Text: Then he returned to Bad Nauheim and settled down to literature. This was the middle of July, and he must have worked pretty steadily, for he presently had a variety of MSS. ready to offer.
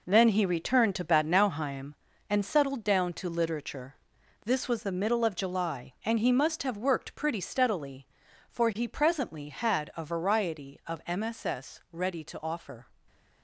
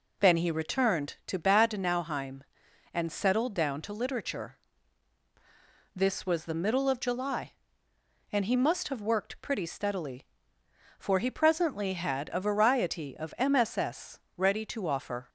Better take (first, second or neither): second